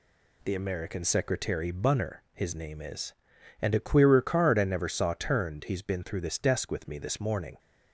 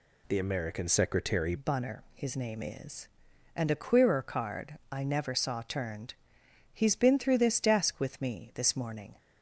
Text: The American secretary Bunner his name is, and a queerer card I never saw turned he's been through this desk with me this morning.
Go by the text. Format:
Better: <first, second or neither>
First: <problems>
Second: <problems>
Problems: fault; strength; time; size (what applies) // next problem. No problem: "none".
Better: first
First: none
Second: changes voice at "Bunner"; from 1.5 s on; 7.6 s long // pauses between "turned" and "he's"; noticeable; at 6.1 s; 0.58 s long